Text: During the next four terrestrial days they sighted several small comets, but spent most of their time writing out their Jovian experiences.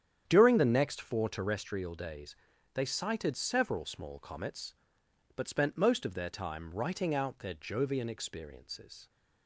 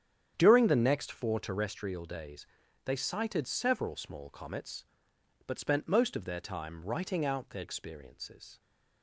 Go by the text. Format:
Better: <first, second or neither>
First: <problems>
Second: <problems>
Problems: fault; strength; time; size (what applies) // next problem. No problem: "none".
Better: first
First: starts louder than the rest; strong; until 1.2 s; 9 dB // pauses between "days" and "they"; at 2.3 s; 0.42 s long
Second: starts louder than the rest; strong; until 1.3 s; 9 dB // pauses between "days" and "they"; at 2.4 s; 0.42 s long // skips "Jovian"; at 7.6 s